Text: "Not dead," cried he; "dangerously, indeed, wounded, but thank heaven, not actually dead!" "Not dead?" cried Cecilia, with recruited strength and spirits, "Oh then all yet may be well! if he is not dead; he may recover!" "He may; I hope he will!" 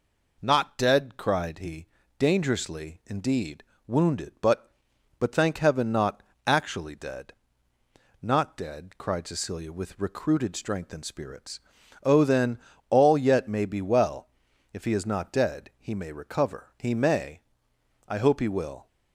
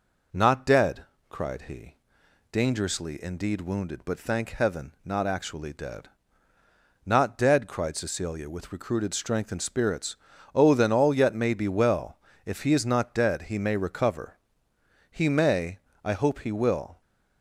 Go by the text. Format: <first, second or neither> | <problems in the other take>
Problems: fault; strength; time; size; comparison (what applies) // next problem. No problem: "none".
second | says "but" twice; at 5.1 s // pauses between "not" and "actually"; slight; at 6.2 s; 0.24 s long // pauses between "then" and "all"; slight; at 12.5 s; 0.32 s long